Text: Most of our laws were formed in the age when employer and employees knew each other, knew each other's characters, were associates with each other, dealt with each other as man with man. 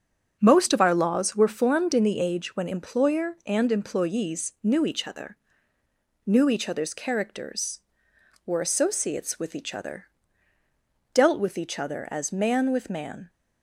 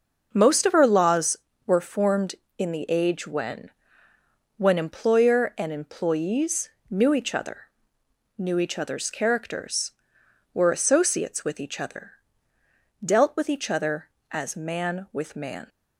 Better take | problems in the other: first | starts louder than the rest; until 1.3 s; 6 dB; also in the first // says "when" twice; at 4.5 s // pauses between "employees" and "knew"; slight; at 6.6 s; 0.20 s long

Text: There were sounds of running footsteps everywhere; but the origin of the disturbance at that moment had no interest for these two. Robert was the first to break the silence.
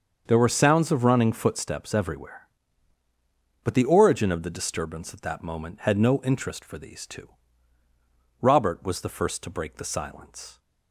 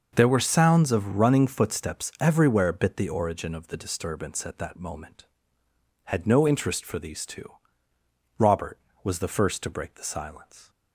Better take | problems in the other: first | starts louder than the rest; noticeable; until 1.1 s; 6 dB; also in the first // says "bit" for "but"; at 2.7 s

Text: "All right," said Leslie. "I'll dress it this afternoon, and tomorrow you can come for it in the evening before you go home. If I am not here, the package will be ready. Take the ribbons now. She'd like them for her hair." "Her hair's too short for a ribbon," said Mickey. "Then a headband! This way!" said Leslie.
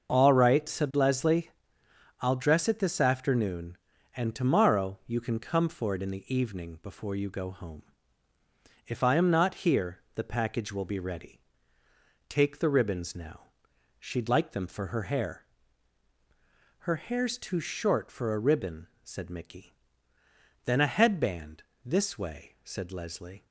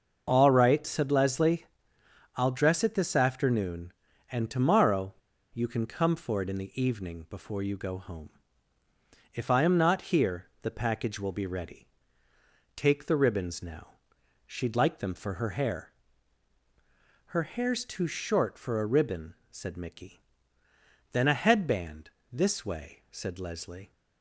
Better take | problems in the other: first | starts louder than the rest; until 1.2 s; 6 dB; also in the first // pauses between "tomorrow" and "you"; at 5.1 s; 0.39 s long

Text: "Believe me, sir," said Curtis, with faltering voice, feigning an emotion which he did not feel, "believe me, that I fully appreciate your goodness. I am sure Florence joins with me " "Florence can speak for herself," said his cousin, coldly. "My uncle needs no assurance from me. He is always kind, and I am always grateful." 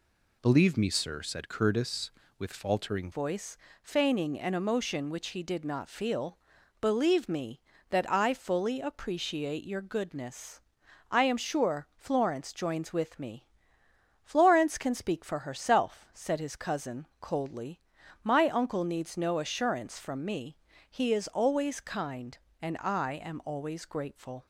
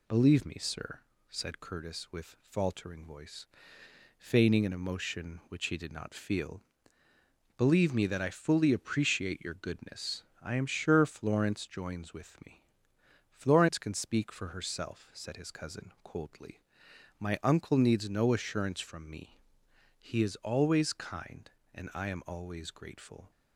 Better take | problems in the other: second | changes voice at "voice"; from 3.1 s on; 21.3 s long

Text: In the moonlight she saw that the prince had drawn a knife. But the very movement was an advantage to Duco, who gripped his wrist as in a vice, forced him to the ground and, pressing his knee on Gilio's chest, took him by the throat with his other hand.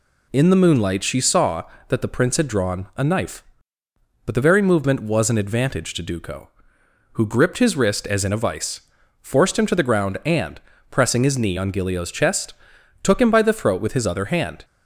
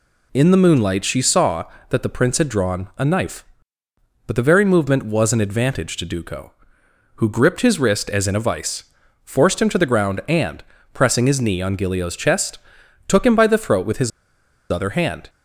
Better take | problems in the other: first | pauses between "his" and "other"; noticeable; at 14.1 s; 0.61 s long

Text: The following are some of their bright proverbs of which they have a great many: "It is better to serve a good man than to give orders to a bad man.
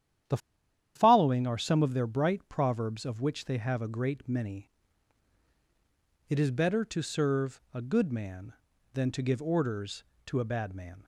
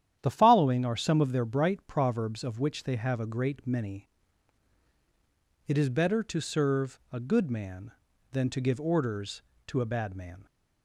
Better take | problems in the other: second | starts louder than the rest; strong; until 1.8 s; 10.5 dB; strong in the second // pauses between "The" and "following"; noticeable; at 0.3 s; 0.58 s long

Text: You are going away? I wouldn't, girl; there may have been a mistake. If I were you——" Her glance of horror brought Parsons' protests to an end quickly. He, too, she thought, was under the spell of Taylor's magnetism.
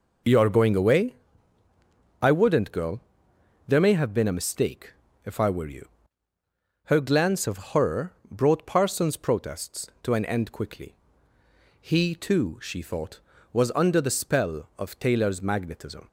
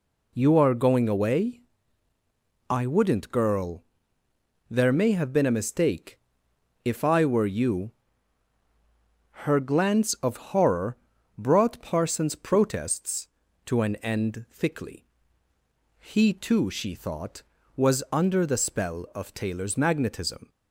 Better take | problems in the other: first | pauses between "horror" and "brought"; at 10.9 s; 0.40 s long; slight in the first // says "thickly" for "quickly"; at 14.4 s

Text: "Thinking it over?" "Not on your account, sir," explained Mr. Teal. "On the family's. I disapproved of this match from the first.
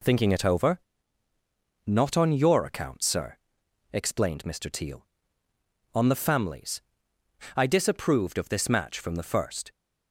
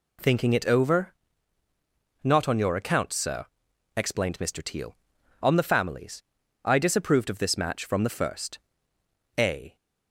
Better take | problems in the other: first | goes on to say "A"; slight; from 9.3 s on; 0.38 s long

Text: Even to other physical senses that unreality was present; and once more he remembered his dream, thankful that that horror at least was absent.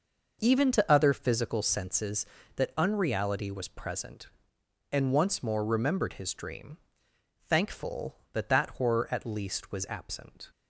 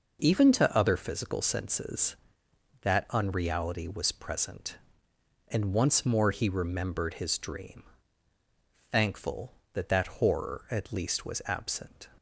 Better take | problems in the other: second | skips "he"; at 5.6 s

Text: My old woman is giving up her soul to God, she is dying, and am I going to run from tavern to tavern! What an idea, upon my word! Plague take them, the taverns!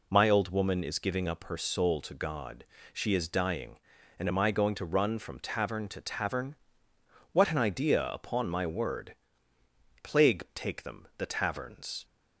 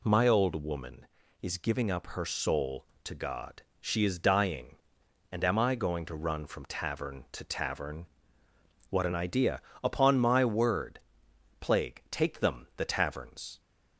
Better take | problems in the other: neither | none

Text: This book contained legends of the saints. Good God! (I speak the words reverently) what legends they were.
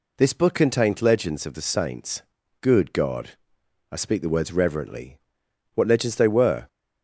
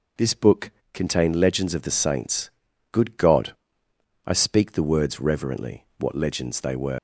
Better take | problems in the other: first | pauses between "book" and "contained"; slight; at 0.7 s; 0.22 s long // leaves "were" unfinished; at 6.9 s; 100 ms

